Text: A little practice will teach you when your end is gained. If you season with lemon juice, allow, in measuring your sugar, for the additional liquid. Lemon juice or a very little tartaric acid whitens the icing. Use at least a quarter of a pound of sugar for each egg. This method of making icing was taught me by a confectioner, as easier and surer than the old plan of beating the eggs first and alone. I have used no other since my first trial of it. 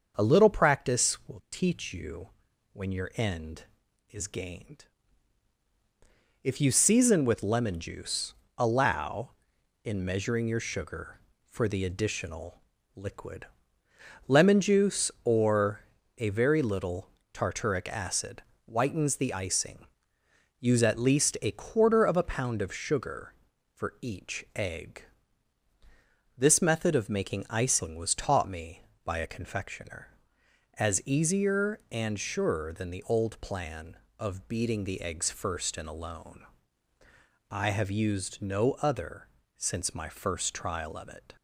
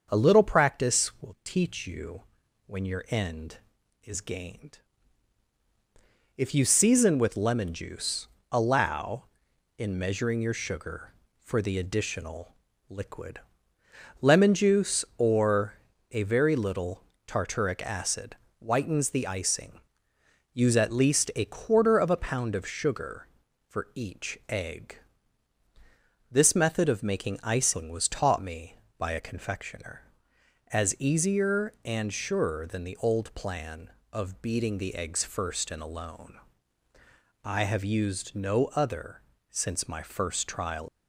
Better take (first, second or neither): first